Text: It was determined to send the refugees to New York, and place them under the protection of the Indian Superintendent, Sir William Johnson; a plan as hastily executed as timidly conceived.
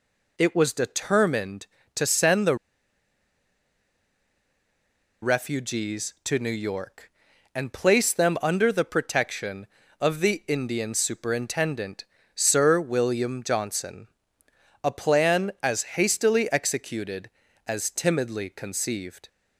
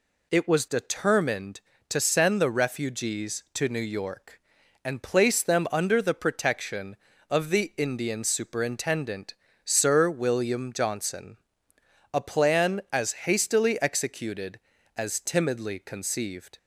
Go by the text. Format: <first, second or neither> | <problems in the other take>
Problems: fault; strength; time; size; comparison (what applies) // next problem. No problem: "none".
second | pauses between "the" and "refugees"; strong; at 2.5 s; 2.6 s long